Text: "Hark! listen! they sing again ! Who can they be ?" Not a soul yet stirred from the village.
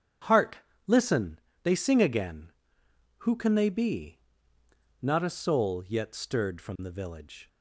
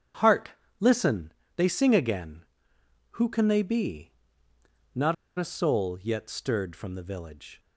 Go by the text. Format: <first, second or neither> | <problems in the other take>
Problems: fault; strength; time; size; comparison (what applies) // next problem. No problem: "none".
first | starts louder than the rest; strong; until 1.7 s; 7.5 dB; strong in the first // pauses between "Not" and "a"; slight; at 5.1 s; 0.24 s long